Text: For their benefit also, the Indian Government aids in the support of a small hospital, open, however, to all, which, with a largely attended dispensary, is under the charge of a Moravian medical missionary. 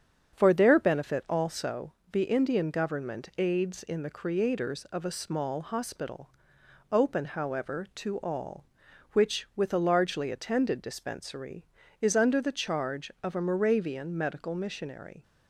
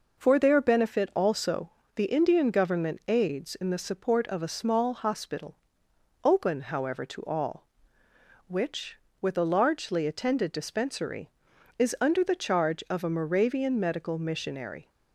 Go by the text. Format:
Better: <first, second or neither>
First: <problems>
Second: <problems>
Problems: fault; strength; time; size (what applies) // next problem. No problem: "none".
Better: second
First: starts louder than the rest; strong; until 1.3 s; 8 dB // says "creators" for "support"; at 4.1 s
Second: none